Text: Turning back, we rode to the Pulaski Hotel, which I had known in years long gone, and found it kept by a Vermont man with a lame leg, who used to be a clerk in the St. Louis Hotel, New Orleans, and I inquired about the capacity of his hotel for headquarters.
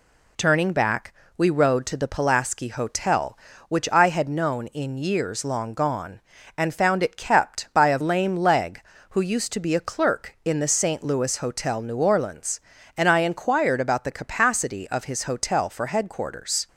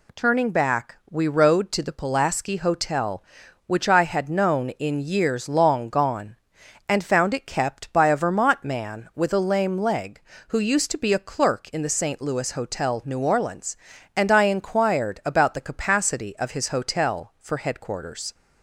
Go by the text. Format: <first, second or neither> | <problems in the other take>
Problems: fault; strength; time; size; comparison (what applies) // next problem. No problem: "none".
second | skips "Vermont man with a"; at 8.0 s